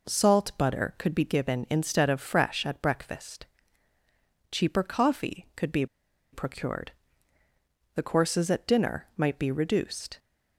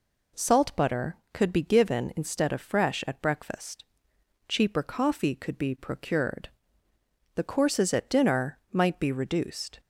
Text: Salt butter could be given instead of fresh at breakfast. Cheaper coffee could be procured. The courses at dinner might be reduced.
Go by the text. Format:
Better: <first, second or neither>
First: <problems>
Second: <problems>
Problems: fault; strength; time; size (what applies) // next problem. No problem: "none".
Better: second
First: pauses between "be" and "procured"; noticeable; at 5.8 s; 0.47 s long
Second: none